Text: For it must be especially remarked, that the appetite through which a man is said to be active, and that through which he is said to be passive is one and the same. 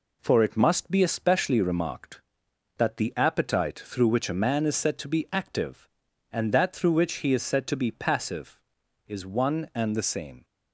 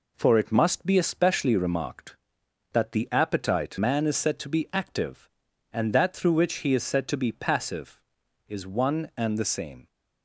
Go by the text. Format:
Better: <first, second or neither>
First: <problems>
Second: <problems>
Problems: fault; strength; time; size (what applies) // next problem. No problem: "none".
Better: first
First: none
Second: skips "through which a"; at 3.7 s